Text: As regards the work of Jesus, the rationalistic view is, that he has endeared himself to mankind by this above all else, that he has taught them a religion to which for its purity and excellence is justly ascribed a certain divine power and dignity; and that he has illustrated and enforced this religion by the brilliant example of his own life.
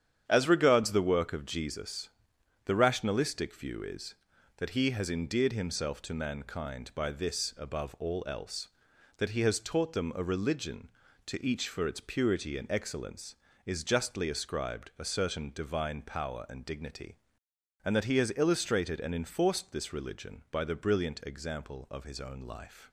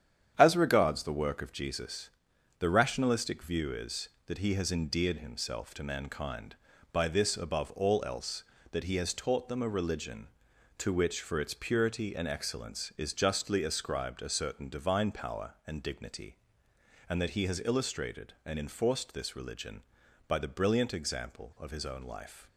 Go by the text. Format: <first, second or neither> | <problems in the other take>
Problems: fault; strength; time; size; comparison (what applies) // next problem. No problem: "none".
second | starts louder than the rest; strong; until 1.2 s; 9 dB; strong in the second // says "each" for "which"; at 11.4 s